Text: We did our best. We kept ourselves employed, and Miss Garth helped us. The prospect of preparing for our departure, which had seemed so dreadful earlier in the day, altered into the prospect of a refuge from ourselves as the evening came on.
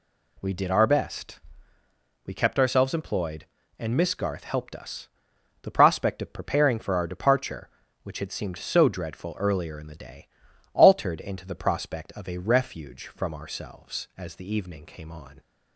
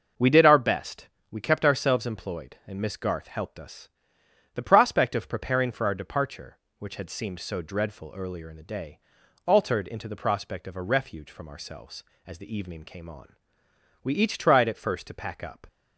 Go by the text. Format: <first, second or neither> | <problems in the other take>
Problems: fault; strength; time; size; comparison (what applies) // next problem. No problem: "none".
first | starts louder than the rest; noticeable; until 1.3 s; 6 dB // goes on to say "We each tried at first to pack up"; from 14.0 s on; 1.6 s long